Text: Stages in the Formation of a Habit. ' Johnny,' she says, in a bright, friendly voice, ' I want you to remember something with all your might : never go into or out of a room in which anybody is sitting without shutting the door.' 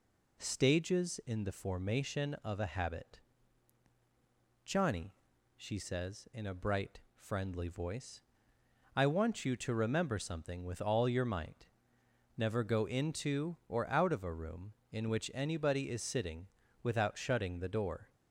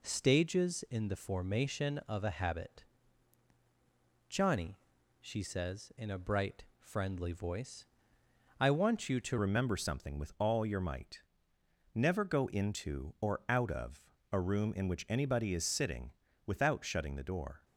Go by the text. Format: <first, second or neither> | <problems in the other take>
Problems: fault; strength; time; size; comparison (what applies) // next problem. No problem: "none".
first | changes voice at "remember"; from 9.3 s on; 8.3 s long // pauses between "of" and "a"; slight; at 14.0 s; 0.24 s long // pauses between "sitting" and "without"; slight; at 16.1 s; 0.36 s long; slight in the first